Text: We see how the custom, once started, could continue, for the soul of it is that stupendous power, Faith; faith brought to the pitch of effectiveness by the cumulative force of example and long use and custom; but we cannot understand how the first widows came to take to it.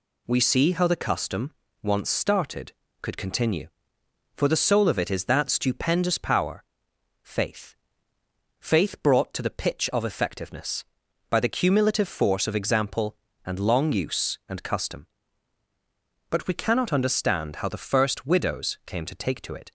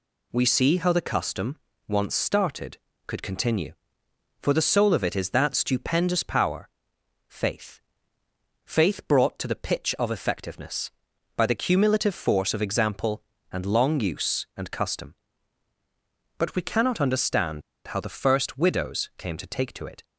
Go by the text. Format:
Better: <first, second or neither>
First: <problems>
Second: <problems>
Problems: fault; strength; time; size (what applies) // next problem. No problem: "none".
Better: first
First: none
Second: pauses between "understand" and "how"; slight; at 17.6 s; 0.25 s long